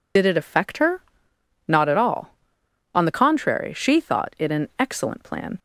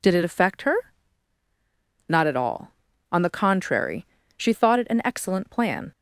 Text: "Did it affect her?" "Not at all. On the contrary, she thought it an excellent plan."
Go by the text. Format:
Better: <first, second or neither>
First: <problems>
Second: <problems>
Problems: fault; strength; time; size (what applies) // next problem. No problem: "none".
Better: second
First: loses the start of "Did"; at 0.1 s; 55 ms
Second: none